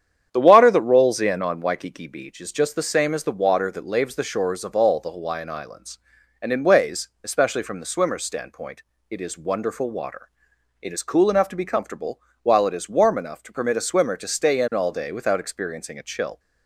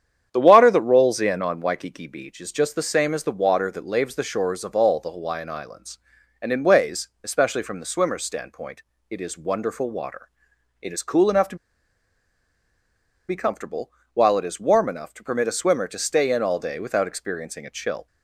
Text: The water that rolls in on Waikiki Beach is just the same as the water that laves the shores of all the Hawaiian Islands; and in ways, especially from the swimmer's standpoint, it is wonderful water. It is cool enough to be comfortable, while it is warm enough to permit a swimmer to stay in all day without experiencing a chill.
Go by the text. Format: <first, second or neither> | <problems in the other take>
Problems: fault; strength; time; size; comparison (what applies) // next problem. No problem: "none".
first | starts louder than the rest; strong; until 1.3 s; 9 dB; strong in the first // pauses between "to" and "be"; strong; at 11.5 s; 1.7 s long